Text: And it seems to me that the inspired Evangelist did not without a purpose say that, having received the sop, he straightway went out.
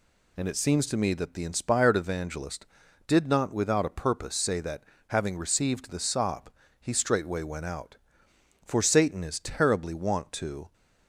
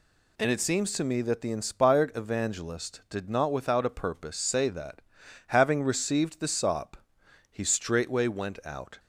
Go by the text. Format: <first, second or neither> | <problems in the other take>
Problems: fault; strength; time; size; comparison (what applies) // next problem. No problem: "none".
second | goes on to say "For Satan is terribly wont to"; strong; from 8.6 s on; 2.0 s long